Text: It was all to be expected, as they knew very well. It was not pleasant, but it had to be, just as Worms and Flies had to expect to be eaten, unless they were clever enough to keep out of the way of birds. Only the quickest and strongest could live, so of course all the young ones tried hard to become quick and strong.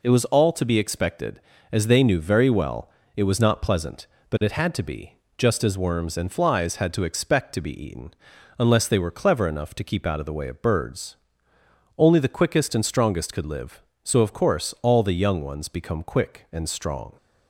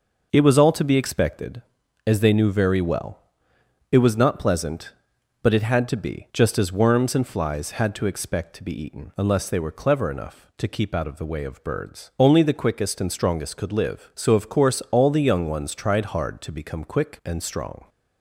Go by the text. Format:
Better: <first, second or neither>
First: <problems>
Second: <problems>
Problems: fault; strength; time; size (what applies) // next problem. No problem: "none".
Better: second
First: skips "tried hard to"; at 15.6 s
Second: none